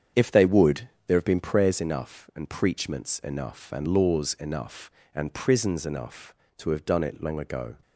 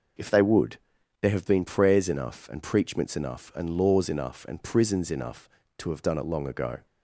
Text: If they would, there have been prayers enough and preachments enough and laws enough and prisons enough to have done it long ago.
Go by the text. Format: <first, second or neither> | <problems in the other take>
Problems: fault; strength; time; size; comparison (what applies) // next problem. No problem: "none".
second | starts louder than the rest; strong; until 1.8 s; 8 dB